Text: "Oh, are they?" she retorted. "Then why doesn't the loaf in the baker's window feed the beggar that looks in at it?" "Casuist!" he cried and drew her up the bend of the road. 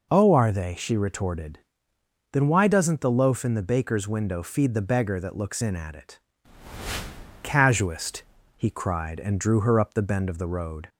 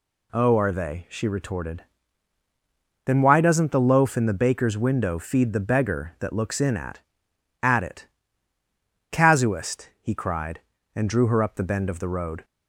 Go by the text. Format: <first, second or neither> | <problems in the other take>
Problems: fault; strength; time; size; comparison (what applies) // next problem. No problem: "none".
first | says "at" twice; at 7.6 s